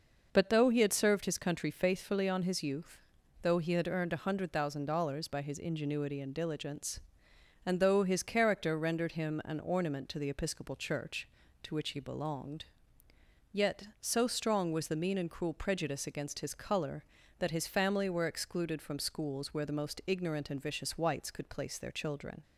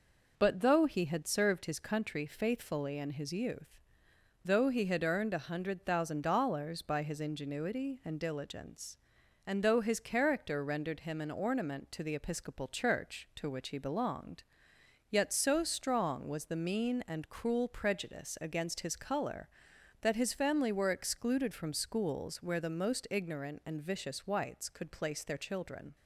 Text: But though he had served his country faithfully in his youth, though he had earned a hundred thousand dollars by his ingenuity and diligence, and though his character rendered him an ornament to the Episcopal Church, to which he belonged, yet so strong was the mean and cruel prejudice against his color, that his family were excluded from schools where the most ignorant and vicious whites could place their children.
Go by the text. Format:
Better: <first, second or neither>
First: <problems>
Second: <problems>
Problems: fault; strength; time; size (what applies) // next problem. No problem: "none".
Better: second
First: says "on" for "in"; at 2.2 s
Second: none